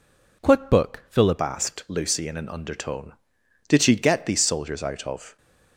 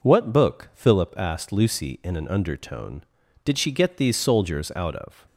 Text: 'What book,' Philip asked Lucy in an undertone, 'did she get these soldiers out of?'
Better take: second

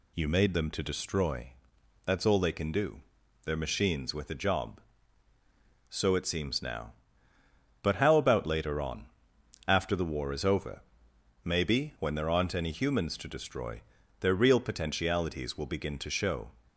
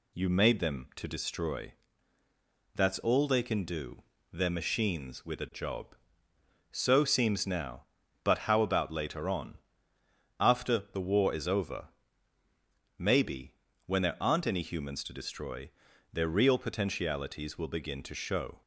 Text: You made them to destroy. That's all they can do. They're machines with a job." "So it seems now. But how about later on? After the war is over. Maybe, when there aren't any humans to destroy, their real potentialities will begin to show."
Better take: first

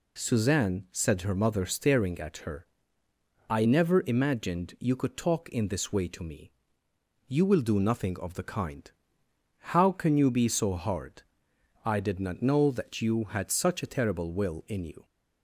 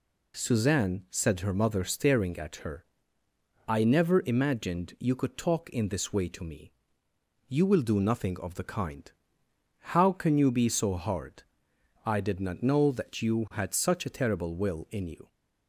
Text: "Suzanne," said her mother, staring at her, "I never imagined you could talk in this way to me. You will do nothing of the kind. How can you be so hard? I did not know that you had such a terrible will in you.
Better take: neither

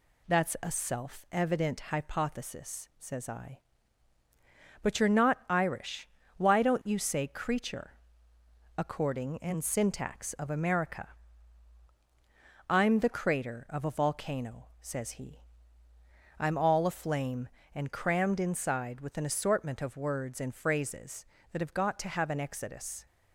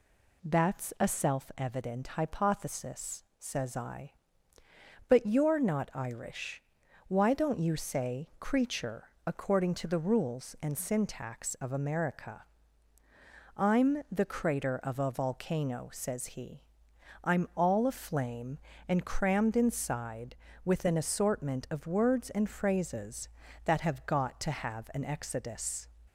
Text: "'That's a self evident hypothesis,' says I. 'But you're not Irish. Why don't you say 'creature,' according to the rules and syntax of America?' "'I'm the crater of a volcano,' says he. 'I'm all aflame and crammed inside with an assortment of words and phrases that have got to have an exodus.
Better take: second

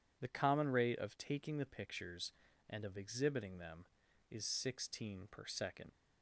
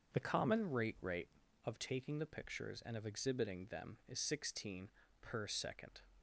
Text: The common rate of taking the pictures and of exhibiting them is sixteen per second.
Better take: first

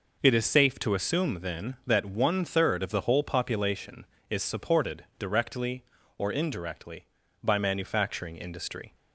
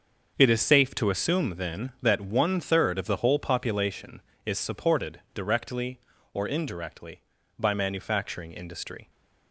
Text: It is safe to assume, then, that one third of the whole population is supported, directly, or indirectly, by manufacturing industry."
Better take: first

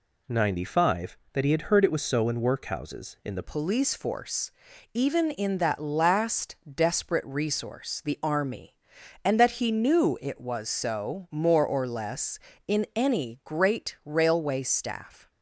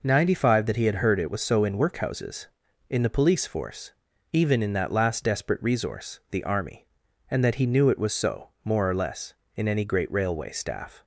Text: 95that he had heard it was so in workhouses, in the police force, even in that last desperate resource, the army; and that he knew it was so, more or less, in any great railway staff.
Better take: second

